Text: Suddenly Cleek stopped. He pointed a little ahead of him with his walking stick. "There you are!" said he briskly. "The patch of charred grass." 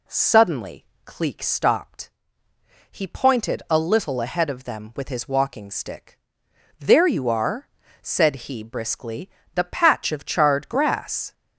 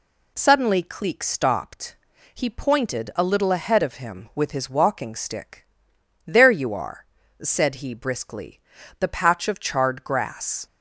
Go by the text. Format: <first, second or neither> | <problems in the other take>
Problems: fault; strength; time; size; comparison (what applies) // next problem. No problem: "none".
second | pauses between "Suddenly" and "Cleek"; slight; at 0.8 s; 0.20 s long // says "them" for "him"; at 4.6 s